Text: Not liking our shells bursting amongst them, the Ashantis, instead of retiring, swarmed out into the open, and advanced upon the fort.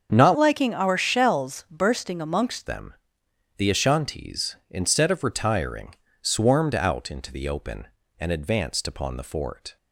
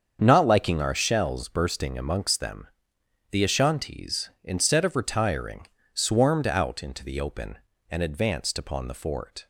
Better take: second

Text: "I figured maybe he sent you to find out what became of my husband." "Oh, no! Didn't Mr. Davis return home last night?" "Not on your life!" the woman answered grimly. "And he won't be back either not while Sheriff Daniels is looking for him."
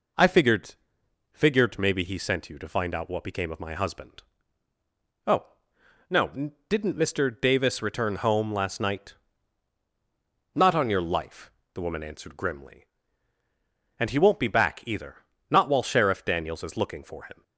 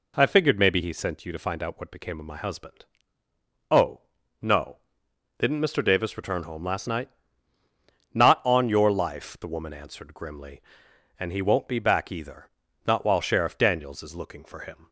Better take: second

